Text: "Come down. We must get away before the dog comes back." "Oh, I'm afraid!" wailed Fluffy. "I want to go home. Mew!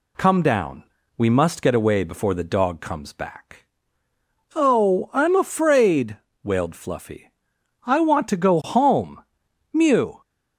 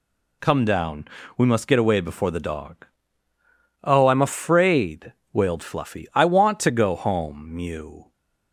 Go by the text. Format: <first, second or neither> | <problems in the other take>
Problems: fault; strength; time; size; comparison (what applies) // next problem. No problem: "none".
first | skips "comes back"; at 3.3 s